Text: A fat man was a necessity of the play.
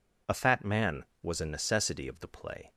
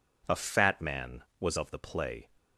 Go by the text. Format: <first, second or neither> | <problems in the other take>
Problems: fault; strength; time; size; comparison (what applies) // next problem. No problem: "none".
first | skips "a necessity"; at 1.5 s